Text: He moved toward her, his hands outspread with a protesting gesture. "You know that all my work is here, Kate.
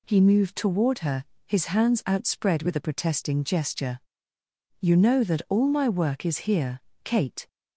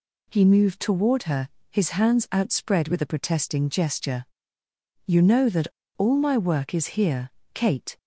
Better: first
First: none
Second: pauses between "that" and "all"; slight; at 5.6 s; 0.29 s long

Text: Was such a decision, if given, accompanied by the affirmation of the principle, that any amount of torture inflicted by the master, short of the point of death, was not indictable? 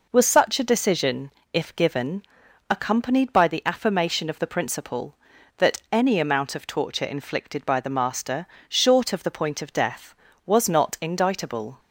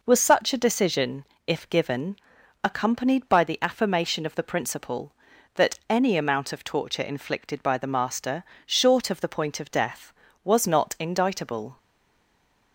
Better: first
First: none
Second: stays silent after the last word; from 11.7 s on; 1.0 s long

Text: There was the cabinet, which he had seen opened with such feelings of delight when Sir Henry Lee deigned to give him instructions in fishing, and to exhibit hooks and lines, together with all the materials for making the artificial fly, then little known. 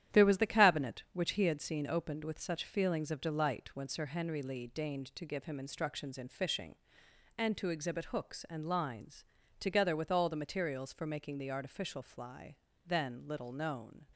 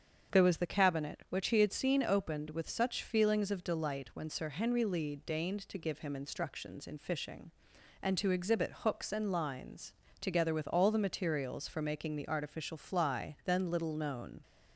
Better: second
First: gets quieter; throughout; 6.5 dB // starts louder than the rest; strong; until 1.2 s; 11 dB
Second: starts louder than the rest; strong; until 1.4 s; 7 dB

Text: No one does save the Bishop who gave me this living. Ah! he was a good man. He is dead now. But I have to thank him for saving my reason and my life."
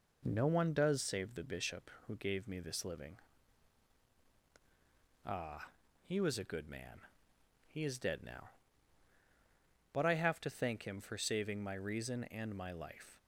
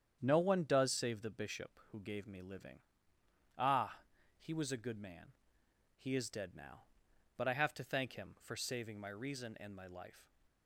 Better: first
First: none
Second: starts louder than the rest; strong; until 1.2 s; 8.5 dB // skips "this"; at 2.4 s

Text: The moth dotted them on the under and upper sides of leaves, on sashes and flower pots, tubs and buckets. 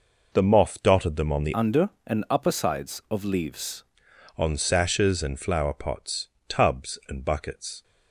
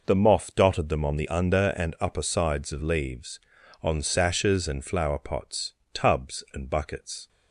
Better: second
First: changes voice from "under" to "leaves"; from 1.5 to 3.8 s; 2.3 s long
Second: none

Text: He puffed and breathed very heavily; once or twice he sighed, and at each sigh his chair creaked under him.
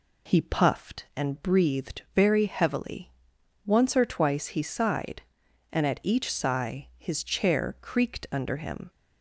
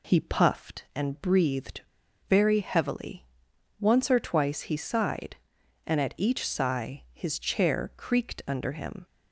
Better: first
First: none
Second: pauses between "breathed" and "very"; noticeable; at 1.7 s; 0.49 s long

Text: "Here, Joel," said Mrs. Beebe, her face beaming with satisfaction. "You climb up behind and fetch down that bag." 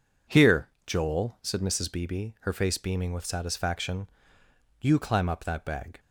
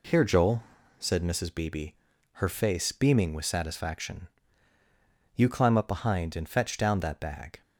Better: second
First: skips "behind and fetch down"; at 5.4 s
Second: none

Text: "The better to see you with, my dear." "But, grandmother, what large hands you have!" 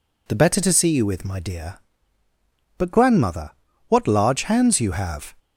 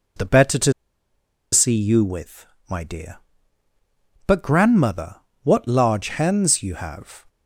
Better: first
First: none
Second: pauses between "to" and "see"; noticeable; at 0.7 s; 0.80 s long

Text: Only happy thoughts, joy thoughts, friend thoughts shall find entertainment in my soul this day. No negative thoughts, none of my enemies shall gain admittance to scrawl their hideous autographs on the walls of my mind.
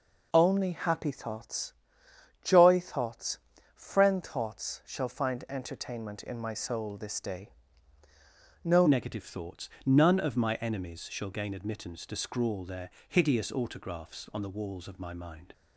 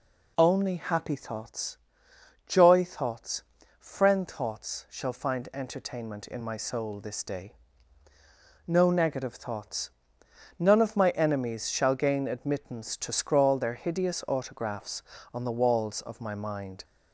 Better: second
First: changes voice at "negative"; from 8.8 s on; 6.7 s long // pauses between "their" and "hideous"; slight; at 12.8 s; 0.20 s long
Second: none

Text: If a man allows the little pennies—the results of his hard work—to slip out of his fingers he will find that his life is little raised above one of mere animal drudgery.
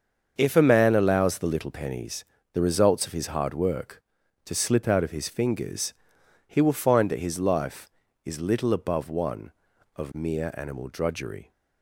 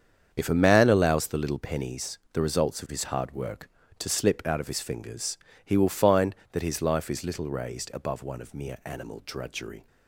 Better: second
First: starts louder than the rest; until 1.3 s; 7 dB // pauses between "fingers" and "he"; noticeable; at 5.9 s; 0.52 s long // skips "raised"; at 8.7 s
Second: starts louder than the rest; strong; until 1.3 s; 7.5 dB // pauses between "fingers" and "he"; slight; at 5.3 s; 0.26 s long

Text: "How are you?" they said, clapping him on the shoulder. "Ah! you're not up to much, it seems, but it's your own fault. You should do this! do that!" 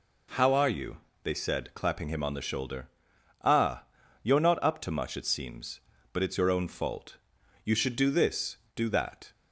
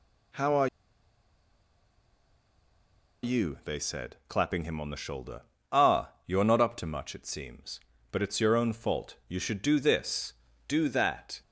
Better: first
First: none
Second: pauses between "are" and "you"; strong; at 0.6 s; 2.5 s long

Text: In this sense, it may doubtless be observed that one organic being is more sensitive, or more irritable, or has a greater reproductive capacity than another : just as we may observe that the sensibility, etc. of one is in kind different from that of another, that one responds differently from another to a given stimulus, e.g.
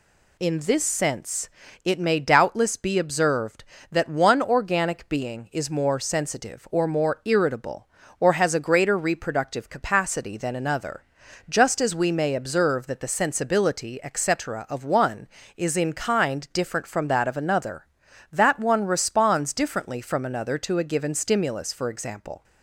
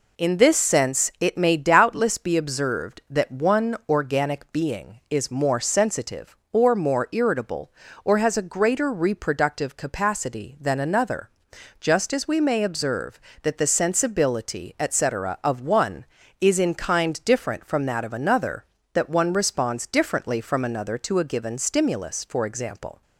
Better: neither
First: none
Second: none

